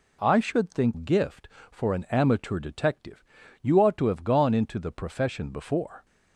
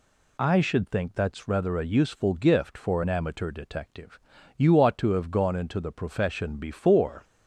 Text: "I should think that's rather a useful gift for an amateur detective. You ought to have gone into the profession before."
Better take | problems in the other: second | skips "that's rather a useful"; at 0.9 s

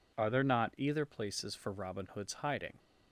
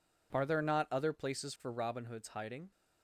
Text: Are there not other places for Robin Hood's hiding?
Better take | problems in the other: second | says "either" for "other"; at 0.7 s

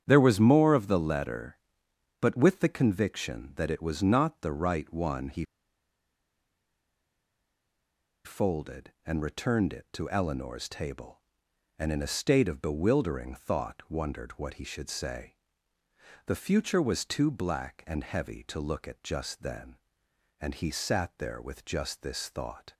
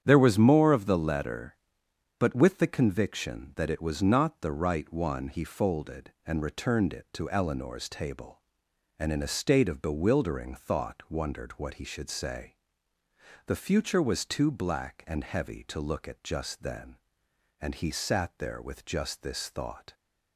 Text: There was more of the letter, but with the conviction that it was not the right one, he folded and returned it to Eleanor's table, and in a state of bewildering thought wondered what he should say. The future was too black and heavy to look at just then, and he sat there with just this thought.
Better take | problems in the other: second | starts louder than the rest; strong; until 1.0 s; 9 dB; strong in the second // pauses between "he" and "folded"; strong; at 5.4 s; 2.8 s long

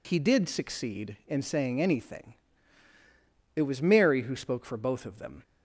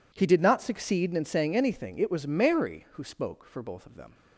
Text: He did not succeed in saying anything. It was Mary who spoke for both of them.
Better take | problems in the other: second | skips "not"; at 0.4 s

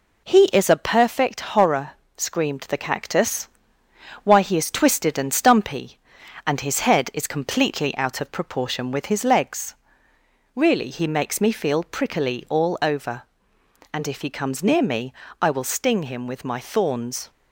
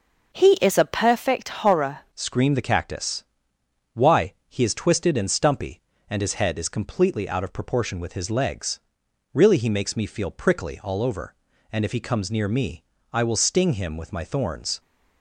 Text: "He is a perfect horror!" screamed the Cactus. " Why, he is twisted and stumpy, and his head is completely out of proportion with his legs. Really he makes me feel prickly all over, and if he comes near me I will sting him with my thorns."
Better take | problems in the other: first | changes voice at "screamed"; from 2.1 s on; 12.6 s long // pauses between "me" and "I"; slight; at 12.8 s; 0.30 s long; slight in the first

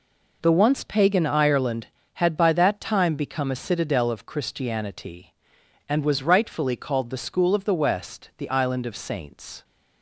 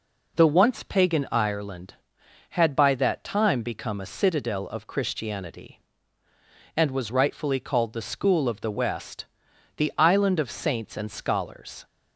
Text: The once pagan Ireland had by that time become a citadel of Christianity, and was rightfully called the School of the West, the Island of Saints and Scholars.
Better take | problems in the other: second | stops before "and Scholars"; at 9.6 s

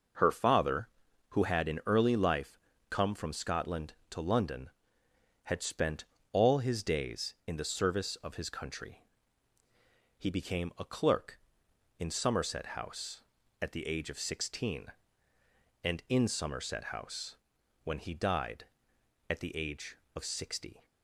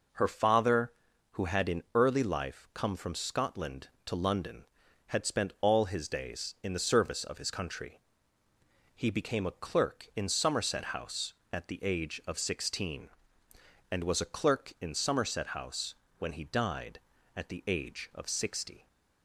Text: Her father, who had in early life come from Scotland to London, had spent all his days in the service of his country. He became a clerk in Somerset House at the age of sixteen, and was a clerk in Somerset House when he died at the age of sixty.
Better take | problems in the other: second | pauses between "life" and "come"; slight; at 2.5 s; 0.30 s long // pauses between "spent" and "all"; slight; at 6.0 s; 0.26 s long // skips "was a clerk"; at 16.0 s // pauses between "House" and "when"; noticeable; at 17.3 s; 0.48 s long; slight in the second

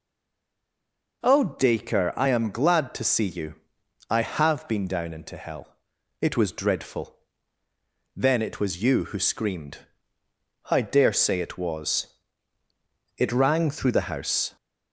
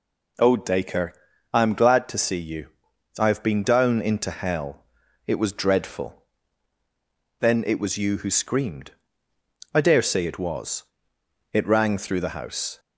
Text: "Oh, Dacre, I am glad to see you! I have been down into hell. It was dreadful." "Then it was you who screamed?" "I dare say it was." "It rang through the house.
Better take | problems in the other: second | stays silent before the first word; noticeable; until 1.2 s; 1.2 s long

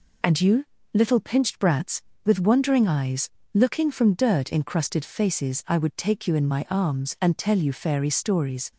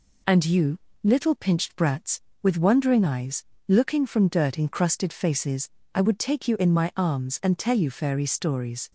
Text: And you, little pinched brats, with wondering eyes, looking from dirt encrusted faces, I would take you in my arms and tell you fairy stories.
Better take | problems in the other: neither | none

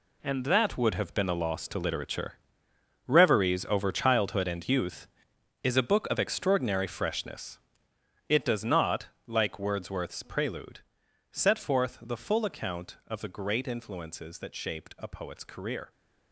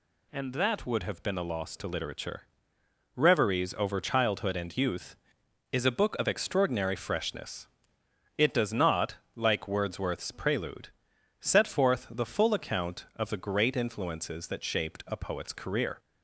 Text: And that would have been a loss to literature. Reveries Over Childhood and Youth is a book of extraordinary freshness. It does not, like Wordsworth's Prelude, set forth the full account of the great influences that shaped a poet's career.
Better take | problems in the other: second | gets quieter; strong; throughout; 11 dB

